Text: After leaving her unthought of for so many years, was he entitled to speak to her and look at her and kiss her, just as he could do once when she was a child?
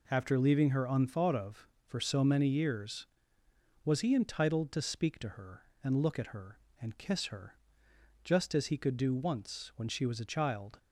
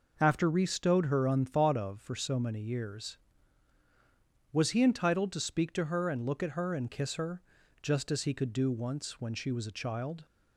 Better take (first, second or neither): first